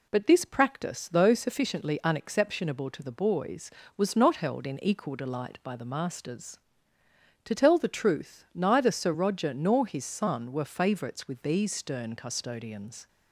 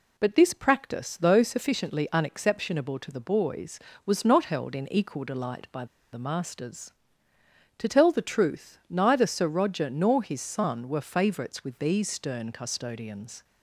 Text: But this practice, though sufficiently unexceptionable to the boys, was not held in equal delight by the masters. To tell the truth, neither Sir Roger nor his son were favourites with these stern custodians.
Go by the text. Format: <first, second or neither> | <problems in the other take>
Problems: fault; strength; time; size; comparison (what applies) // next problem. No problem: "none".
first | pauses between "by" and "the"; slight; at 5.8 s; 0.29 s long